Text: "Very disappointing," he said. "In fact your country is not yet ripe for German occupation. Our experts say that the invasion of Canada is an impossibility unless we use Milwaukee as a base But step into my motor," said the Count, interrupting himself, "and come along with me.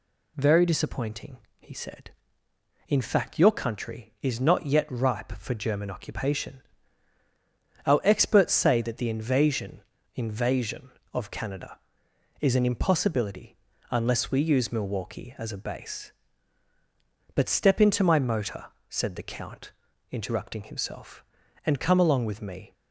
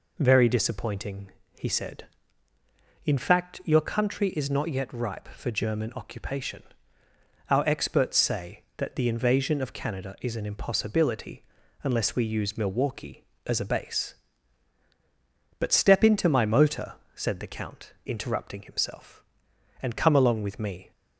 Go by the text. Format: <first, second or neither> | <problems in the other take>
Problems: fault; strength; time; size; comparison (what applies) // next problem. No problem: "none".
second | says "invasion" twice; at 10.1 s // pauses between "impossibility" and "unless"; slight; at 13.5 s; 0.34 s long; also in the second